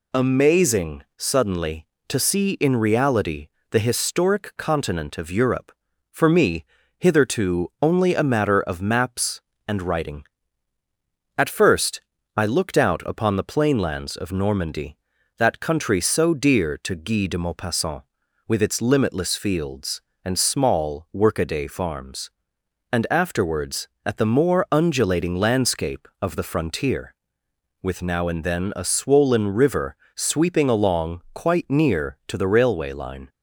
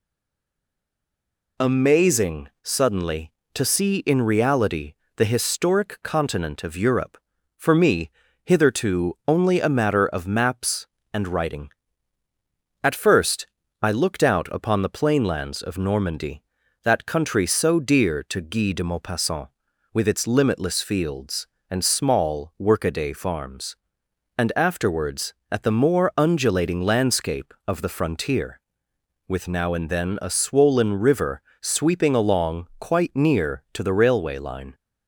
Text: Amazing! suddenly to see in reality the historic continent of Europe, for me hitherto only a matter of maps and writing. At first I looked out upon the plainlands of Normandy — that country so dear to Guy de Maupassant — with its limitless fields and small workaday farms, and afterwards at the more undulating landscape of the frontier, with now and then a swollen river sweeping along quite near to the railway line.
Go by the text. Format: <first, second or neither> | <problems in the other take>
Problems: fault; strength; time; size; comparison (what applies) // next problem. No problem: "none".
first | stays silent before the first word; noticeable; until 1.5 s; 1.5 s long // pauses between "reality" and "the"; slight; at 4.9 s; 0.20 s long; slight in the first // pauses between "me" and "hitherto"; slight; at 8.1 s; 0.32 s long; slight in the first // pauses between "first" and "I"; slight; at 13.4 s; 0.34 s long; slight in the first // pauses between "river" and "sweeping"; slight; at 31.4 s; 0.18 s long; slight in the first